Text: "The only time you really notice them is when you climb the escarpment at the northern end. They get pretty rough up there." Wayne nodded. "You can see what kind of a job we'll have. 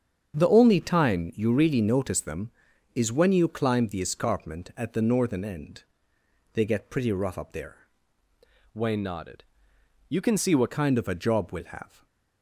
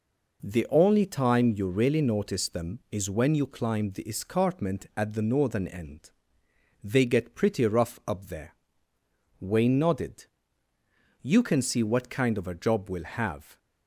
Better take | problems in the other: second | starts louder than the rest; strong; until 1.4 s; 7.5 dB // changes voice from "Wayne" to "what"; from 8.7 to 10.6 s; 1.9 s long // stays silent after the last word; slight; from 11.8 s on; 0.6 s long

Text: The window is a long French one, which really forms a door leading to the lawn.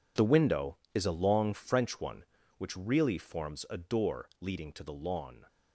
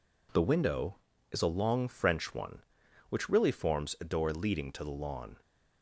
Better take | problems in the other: second | gets quieter; strong; throughout; 13 dB

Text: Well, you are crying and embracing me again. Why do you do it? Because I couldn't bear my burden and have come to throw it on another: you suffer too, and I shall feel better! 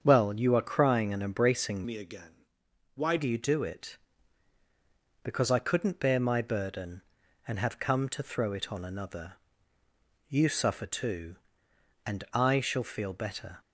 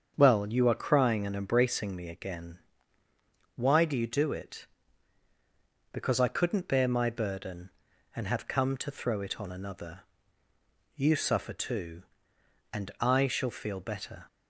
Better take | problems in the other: second | starts louder than the rest; strong; until 1.0 s; 7.5 dB; also in the second // changes voice from "me" to "Why"; from 1.8 to 3.1 s; 1.3 s long

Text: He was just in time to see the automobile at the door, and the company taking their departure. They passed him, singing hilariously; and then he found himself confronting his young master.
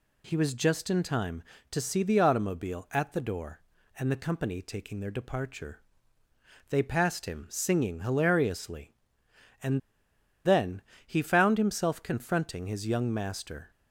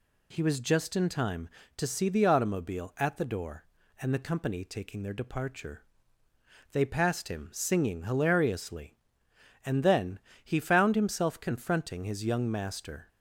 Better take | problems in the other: second | pauses between "and" and "then"; noticeable; at 9.7 s; 0.65 s long // pauses between "then" and "he"; slight; at 10.8 s; 0.24 s long; slight in the second

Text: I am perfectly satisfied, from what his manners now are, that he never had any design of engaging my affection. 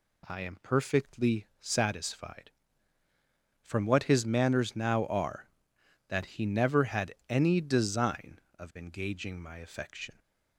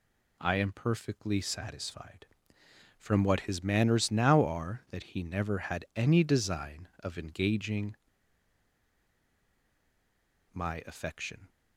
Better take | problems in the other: first | pauses between "engaging" and "my"; strong; at 7.9 s; 2.5 s long

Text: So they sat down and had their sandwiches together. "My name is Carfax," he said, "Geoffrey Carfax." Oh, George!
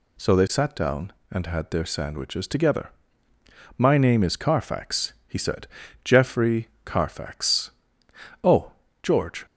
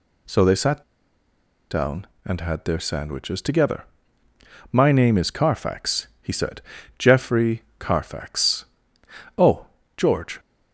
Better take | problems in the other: first | pauses between "sat" and "down"; noticeable; at 0.8 s; 0.88 s long // pauses between "Geoffrey" and "Carfax"; slight; at 7.6 s; 0.16 s long; slight in the first

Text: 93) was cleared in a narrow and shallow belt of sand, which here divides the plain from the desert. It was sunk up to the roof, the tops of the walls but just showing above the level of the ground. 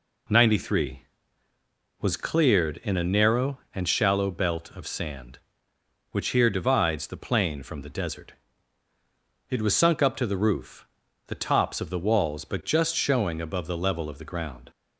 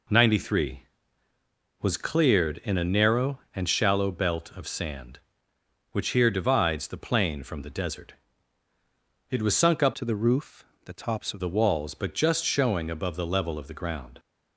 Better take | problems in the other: first | changes voice from "to" to "of"; from 9.9 to 11.4 s; 1.5 s long

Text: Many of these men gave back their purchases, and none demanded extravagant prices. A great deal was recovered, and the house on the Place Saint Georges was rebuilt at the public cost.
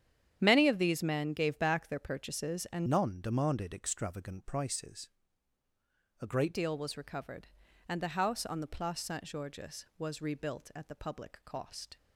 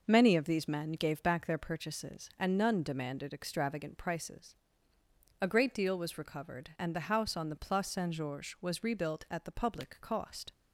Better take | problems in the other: second | starts louder than the rest; strong; until 1.4 s; 9.5 dB // changes voice from "none" to "great"; from 2.8 to 6.5 s; 3.7 s long

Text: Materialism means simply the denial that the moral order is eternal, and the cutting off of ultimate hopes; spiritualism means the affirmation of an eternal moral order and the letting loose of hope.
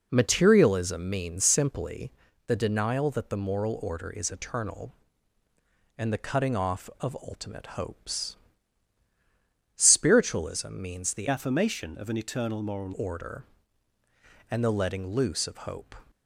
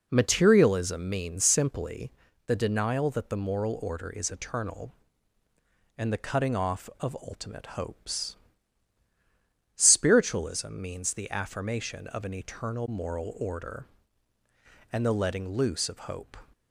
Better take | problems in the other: second | pauses between "simply" and "the"; slight; at 2.1 s; 0.36 s long; slight in the second // changes voice from "affirmation" to "moral"; from 11.2 to 12.9 s; 1.7 s long

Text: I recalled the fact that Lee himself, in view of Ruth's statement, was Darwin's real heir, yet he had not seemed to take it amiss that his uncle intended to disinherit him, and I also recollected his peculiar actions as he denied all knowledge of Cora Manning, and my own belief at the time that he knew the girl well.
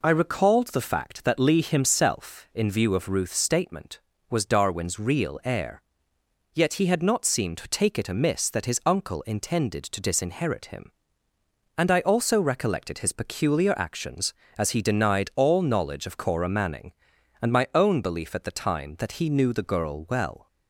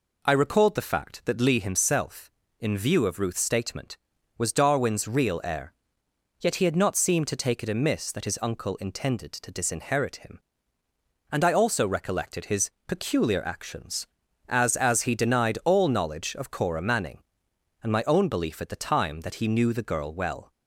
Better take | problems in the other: first | pauses between "his" and "peculiar"; slight; at 12.7 s; 0.16 s long // says "as" twice; at 14.7 s

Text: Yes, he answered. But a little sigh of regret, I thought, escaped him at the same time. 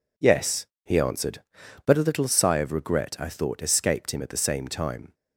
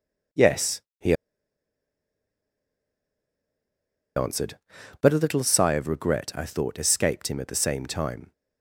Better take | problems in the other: first | pauses between "he" and "answered"; strong; at 1.1 s; 3.0 s long

